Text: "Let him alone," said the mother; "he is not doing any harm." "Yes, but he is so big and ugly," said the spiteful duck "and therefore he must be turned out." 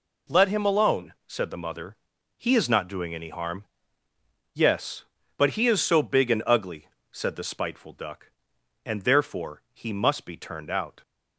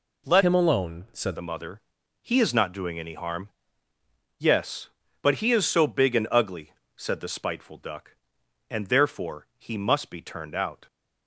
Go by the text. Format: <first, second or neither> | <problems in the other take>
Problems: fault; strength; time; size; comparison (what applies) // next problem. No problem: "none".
first | changes voice from "him" to "said"; from 0.4 to 1.3 s; 0.9 s long